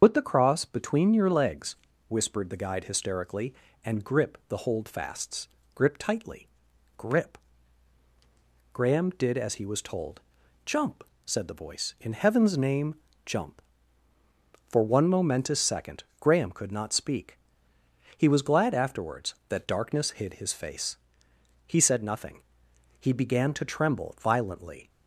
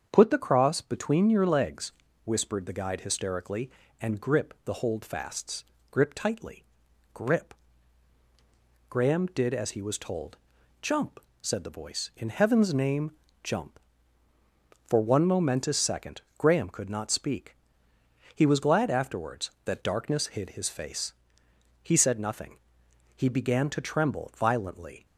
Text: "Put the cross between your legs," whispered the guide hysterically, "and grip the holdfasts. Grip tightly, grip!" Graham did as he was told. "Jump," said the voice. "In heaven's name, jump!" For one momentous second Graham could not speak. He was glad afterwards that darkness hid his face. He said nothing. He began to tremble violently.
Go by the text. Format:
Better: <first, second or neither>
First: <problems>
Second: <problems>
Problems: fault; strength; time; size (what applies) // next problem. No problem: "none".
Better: second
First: loses the start of "Put"; at 0.0 s; 85 ms // starts louder than the rest; until 1.0 s; 6.5 dB // pauses between "second" and "Graham"; slight; at 16.0 s; 0.16 s long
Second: starts louder than the rest; strong; until 1.1 s; 7 dB // pauses between "second" and "Graham"; slight; at 16.2 s; 0.16 s long